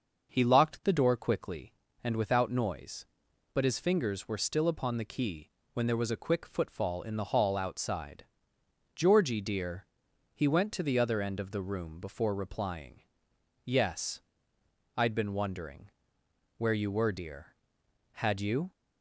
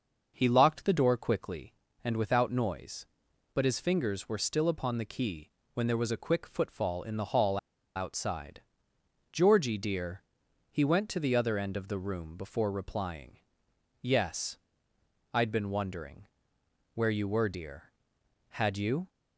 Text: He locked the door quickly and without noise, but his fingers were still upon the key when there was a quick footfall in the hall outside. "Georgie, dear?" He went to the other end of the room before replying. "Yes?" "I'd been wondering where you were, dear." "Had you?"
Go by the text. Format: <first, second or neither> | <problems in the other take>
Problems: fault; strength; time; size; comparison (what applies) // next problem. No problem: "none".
first | pauses between "key" and "when"; slight; at 5.4 s; 0.26 s long; slight in the first // pauses between "hall" and "outside"; at 7.5 s; 0.39 s long // pauses between "wondering" and "where"; noticeable; at 16.2 s; 0.68 s long; noticeable in the first